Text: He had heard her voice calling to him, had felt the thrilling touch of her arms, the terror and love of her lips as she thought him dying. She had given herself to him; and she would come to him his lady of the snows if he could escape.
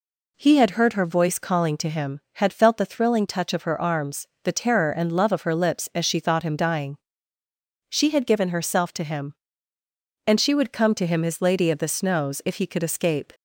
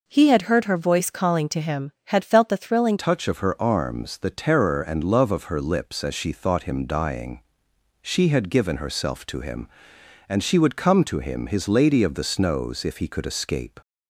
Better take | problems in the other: first | changes voice at "touch"; from 2.9 s on; 10.8 s long

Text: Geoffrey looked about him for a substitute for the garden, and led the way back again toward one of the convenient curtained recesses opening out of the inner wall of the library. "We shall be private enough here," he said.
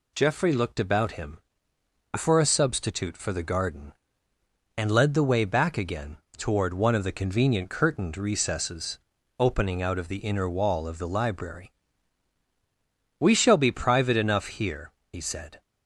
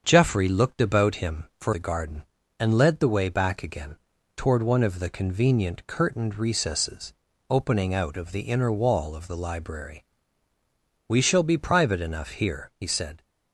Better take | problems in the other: first | starts louder than the rest; strong; until 1.0 s; 7.5 dB // skips "a substitute for"; at 1.7 s // pauses between "again" and "toward"; at 3.9 s; 0.40 s long; slight in the first // pauses between "recesses" and "opening"; slight; at 7.1 s; 0.34 s long; also in the first

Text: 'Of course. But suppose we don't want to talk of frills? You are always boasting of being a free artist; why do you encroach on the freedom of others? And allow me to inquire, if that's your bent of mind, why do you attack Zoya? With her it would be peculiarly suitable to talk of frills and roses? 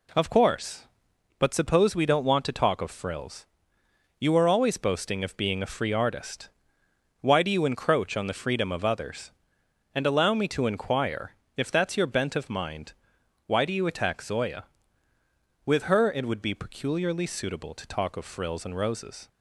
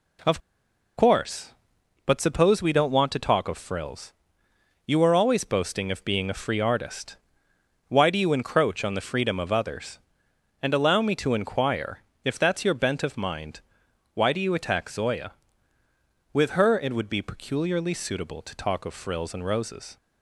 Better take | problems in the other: first | pauses between "Of" and "course"; noticeable; at 0.3 s; 0.57 s long

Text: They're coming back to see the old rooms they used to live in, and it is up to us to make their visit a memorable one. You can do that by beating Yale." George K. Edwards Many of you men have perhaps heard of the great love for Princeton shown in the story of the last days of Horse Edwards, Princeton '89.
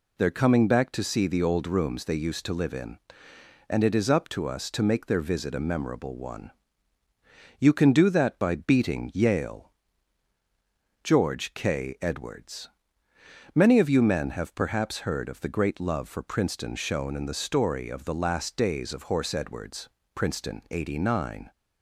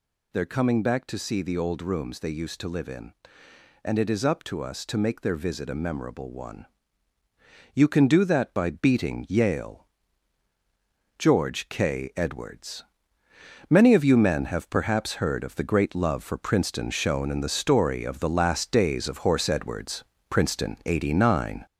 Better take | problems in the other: first | gets louder; noticeable; throughout; 5 dB // pauses between "Edwards" and "Many"; noticeable; at 12.8 s; 0.86 s long; noticeable in the first

